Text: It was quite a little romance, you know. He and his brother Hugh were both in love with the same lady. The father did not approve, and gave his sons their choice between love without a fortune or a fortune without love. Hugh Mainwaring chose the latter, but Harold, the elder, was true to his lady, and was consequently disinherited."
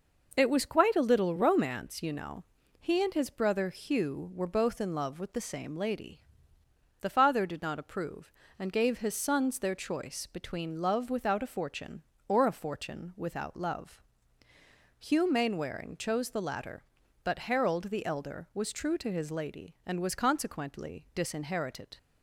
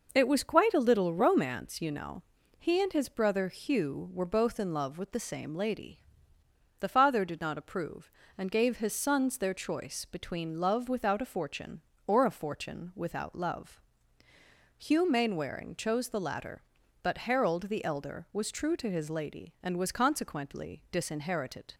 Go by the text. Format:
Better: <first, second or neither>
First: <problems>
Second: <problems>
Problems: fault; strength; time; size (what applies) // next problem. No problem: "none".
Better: neither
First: none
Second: none